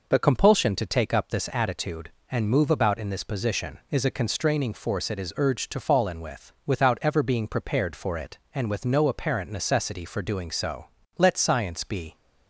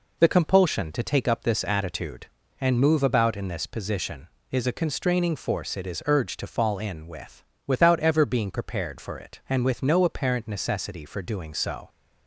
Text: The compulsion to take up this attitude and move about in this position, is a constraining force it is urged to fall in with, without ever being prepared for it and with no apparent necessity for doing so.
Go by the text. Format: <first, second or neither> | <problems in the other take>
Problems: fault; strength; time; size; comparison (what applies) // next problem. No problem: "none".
second | goes on to say "Let science be"; noticeable; from 11.1 s on; 0.96 s long